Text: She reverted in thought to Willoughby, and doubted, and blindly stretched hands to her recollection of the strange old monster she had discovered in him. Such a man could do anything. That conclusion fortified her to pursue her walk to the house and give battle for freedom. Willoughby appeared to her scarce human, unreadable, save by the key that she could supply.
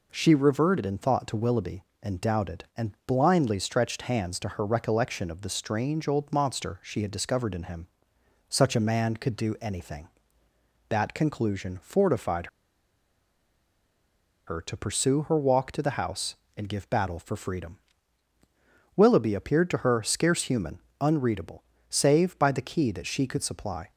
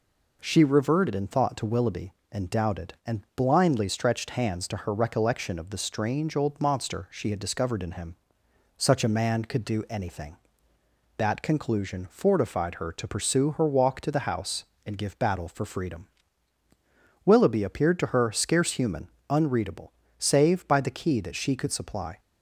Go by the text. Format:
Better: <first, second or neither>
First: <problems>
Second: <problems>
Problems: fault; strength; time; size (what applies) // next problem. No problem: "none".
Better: second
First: pauses between "fortified" and "her"; strong; at 12.4 s; 2.0 s long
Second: none